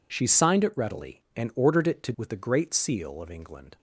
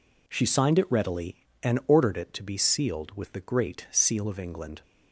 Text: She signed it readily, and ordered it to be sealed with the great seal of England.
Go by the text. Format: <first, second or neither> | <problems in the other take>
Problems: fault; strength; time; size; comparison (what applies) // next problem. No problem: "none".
second | skips "be sealed"; at 2.1 s